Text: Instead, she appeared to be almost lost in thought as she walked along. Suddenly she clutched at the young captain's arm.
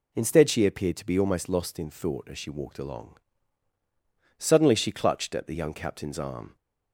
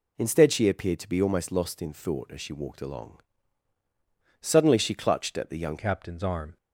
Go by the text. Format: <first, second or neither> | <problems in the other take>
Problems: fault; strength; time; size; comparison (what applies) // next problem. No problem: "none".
first | changes voice at "captain's"; from 5.7 s on; 0.8 s long